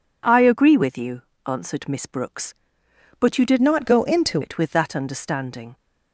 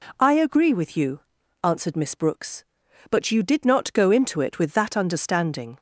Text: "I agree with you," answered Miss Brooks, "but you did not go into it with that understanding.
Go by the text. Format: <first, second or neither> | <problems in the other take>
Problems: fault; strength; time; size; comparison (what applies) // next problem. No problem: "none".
second | changes voice from "not" to "into"; from 3.6 to 4.4 s; 0.8 s long